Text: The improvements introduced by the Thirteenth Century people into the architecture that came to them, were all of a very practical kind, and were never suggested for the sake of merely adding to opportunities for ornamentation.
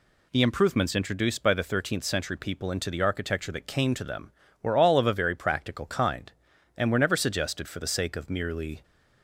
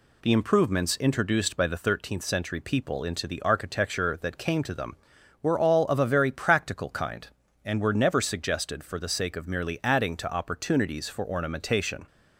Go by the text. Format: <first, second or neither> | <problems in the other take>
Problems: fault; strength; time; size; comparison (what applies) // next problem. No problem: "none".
second | stops before "adding to opportunities for ornamentation"; at 8.8 s